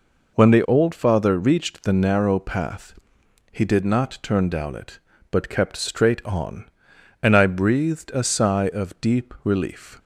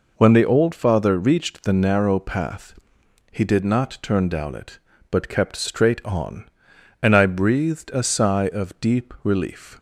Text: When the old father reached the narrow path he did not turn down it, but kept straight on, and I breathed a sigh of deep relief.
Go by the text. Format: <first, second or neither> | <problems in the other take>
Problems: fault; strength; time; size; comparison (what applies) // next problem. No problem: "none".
neither | pauses between "path" and "he"; noticeable; the same in both